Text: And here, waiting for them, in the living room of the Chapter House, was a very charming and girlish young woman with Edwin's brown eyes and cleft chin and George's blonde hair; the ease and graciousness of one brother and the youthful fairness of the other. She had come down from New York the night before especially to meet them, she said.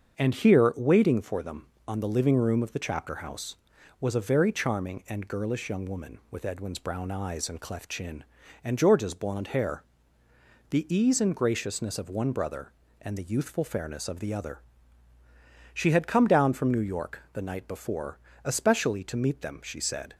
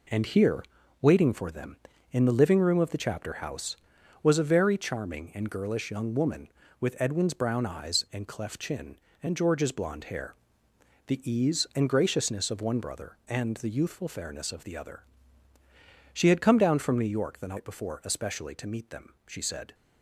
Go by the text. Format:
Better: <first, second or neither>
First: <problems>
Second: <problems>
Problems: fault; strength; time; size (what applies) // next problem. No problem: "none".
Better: second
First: starts louder than the rest; until 1.2 s; 7 dB // says "on" for "in"; at 1.8 s // pauses between "before" and "especially"; slight; at 18.1 s; 0.26 s long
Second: none